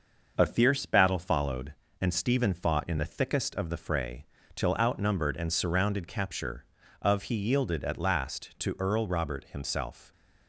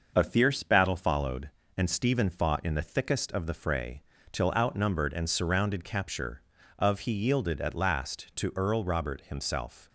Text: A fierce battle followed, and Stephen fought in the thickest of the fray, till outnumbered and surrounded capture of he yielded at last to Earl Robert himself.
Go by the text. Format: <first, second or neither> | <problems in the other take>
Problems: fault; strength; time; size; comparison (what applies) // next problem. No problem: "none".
neither | starts louder than the rest; the same in both